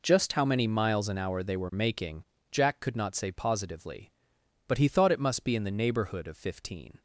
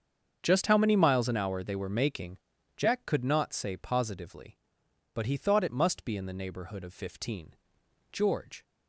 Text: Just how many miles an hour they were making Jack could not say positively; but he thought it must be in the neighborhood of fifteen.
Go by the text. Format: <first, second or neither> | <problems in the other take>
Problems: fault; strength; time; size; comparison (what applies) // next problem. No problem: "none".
first | starts louder than the rest; strong; until 1.4 s; 7 dB // pauses between "making" and "Jack"; at 2.3 s; 0.40 s long; slight in the first // goes on to say "George"; from 8.1 s on; 0.52 s long